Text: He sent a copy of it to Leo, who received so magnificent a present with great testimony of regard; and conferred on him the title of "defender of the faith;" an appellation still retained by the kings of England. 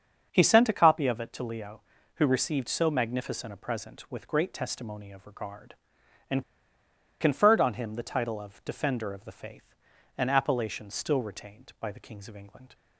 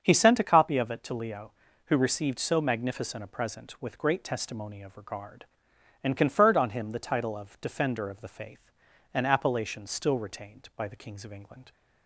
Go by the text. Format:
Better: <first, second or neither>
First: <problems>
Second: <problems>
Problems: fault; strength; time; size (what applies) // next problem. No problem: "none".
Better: second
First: starts louder than the rest; until 1.3 s; 7 dB // pauses between "and" and "conferred"; noticeable; at 6.4 s; 0.77 s long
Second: starts louder than the rest; until 1.0 s; 7 dB